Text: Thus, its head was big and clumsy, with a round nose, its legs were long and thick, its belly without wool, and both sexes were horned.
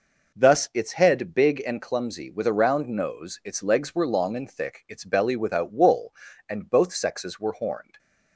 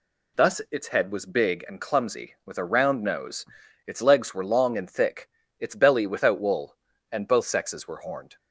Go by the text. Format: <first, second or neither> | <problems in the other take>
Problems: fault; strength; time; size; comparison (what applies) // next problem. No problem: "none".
second | skips "was"; at 1.3 s